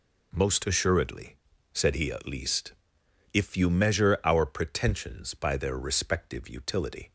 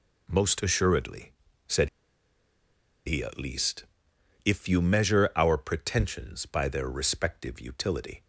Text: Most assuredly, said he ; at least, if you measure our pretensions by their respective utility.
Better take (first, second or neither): first